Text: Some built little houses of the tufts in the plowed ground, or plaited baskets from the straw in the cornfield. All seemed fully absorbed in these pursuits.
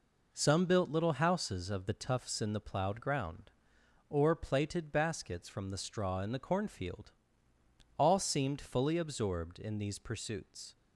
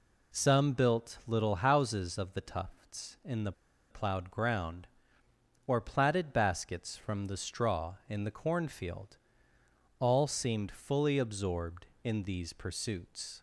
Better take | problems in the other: first | pauses between "the" and "plowed"; at 3.5 s; 0.37 s long

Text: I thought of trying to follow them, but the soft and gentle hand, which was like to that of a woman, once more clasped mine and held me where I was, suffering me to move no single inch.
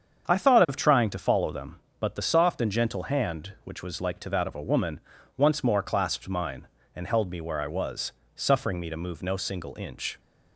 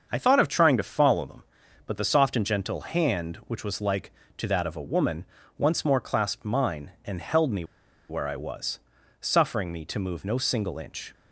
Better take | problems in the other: first | starts louder than the rest; until 1.1 s; 7 dB; strong in the first // pauses between "me" and "where"; at 7.6 s; 0.45 s long

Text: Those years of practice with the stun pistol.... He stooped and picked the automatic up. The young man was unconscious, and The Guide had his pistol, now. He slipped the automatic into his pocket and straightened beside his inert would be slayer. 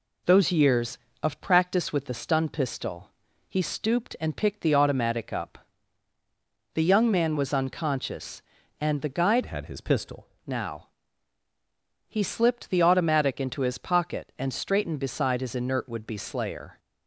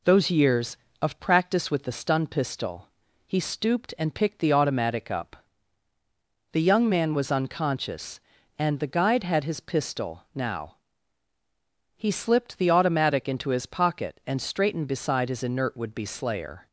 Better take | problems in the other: second | changes voice from "had" to "pistol"; from 9.4 to 10.2 s; 0.8 s long

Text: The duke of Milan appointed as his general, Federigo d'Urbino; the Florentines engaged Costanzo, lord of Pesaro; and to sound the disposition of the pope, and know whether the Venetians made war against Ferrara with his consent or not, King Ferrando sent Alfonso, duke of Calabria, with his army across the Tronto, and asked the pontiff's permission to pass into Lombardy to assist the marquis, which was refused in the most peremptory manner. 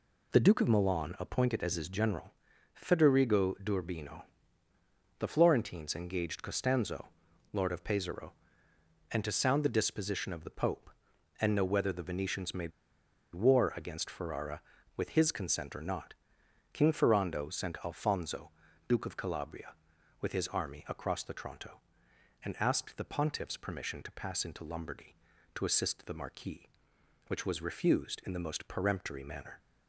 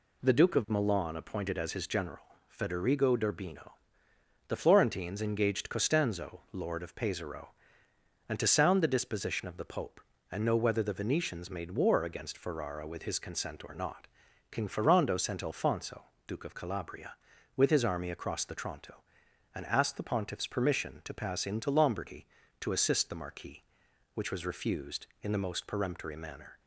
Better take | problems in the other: second | pauses between "made" and "war"; noticeable; at 12.7 s; 0.63 s long

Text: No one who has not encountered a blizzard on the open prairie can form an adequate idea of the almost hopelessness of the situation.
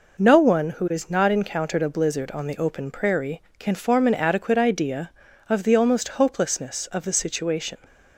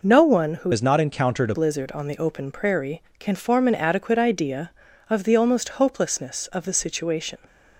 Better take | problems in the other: first | changes voice from "has" to "a"; from 0.7 to 1.5 s; 0.8 s long

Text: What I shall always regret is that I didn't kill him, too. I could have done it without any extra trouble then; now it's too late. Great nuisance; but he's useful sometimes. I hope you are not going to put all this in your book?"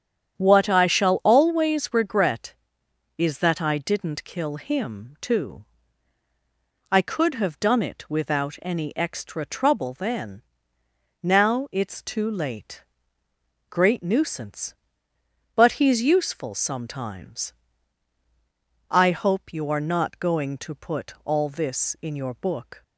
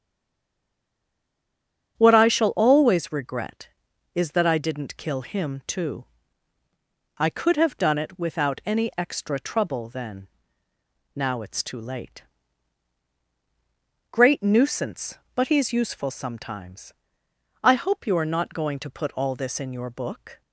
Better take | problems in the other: first | stays silent before the first word; noticeable; until 1.9 s; 1.9 s long // starts louder than the rest; strong; until 2.9 s; 8 dB; strong in the first

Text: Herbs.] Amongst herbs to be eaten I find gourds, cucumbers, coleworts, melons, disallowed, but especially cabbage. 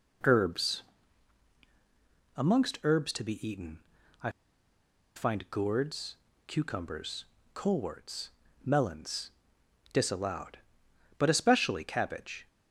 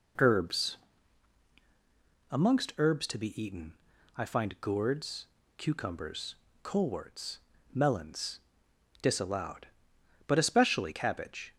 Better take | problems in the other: second | pauses between "eaten" and "I"; at 3.7 s; 0.42 s long; also in the second // pauses between "I" and "find"; noticeable; at 4.2 s; 0.86 s long

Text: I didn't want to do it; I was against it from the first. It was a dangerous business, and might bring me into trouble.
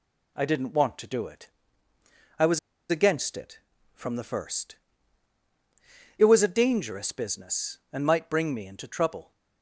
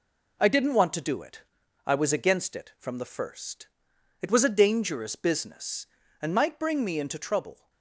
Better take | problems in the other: second | pauses between "was" and "against"; slight; at 2.5 s; 0.30 s long

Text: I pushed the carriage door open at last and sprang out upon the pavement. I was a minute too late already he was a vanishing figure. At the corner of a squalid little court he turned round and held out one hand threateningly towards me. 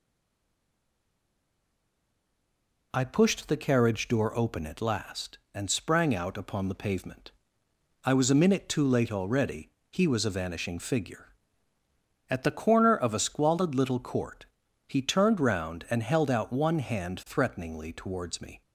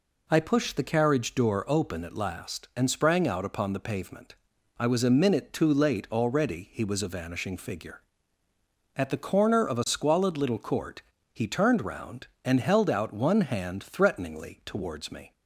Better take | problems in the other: second | stays silent before the first word; strong; until 2.9 s; 2.9 s long // pauses between "already" and "he"; slight; at 9.6 s; 0.24 s long // pauses between "court" and "he"; at 14.4 s; 0.44 s long; slight in the second

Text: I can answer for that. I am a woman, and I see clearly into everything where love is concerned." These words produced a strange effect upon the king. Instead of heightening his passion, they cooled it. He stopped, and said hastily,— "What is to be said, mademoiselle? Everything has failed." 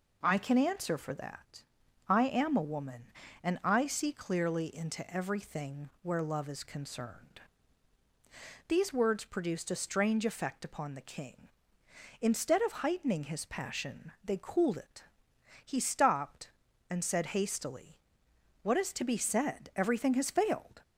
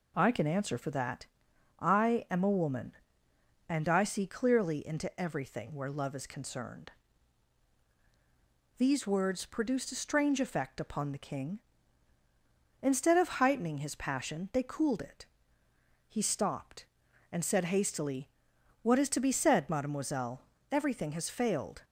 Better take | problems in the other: second | skips "mademoiselle"; at 19.7 s

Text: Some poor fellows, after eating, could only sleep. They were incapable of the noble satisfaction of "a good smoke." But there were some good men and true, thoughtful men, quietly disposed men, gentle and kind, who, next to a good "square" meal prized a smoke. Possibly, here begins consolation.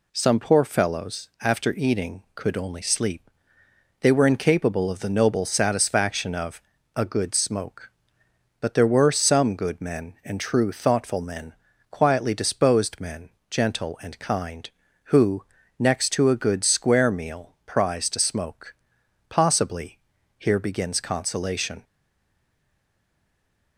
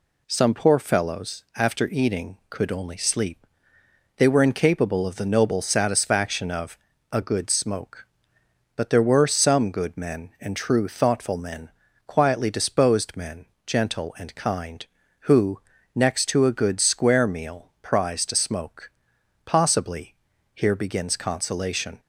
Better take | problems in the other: second | pauses between "of" and "a"; slight; at 6.6 s; 0.34 s long; slight in the second // stays silent after the last word; noticeable; from 21.8 s on; 1.9 s long

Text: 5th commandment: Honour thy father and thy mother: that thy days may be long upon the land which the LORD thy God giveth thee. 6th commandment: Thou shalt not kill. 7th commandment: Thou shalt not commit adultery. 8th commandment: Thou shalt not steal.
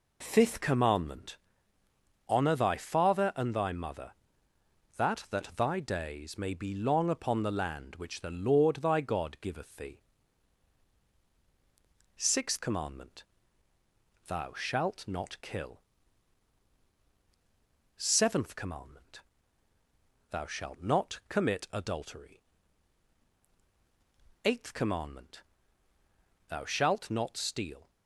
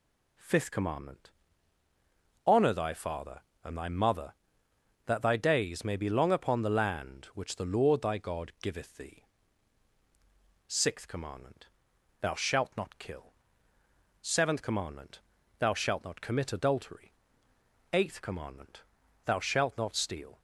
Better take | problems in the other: second | says "that" twice; at 5.2 s

